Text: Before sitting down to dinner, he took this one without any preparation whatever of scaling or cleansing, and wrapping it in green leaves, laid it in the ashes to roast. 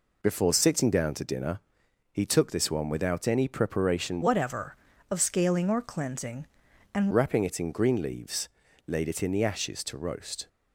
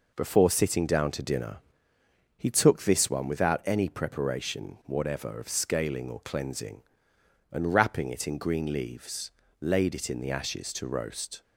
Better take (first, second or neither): second